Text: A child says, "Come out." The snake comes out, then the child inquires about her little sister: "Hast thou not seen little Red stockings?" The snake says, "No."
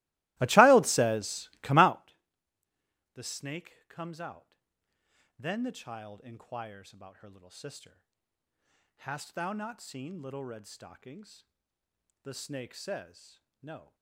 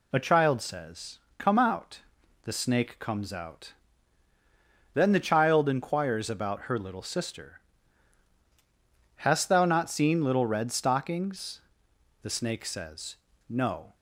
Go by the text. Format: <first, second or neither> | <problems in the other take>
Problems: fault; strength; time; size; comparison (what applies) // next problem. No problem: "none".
second | starts louder than the rest; strong; until 2.1 s; 20 dB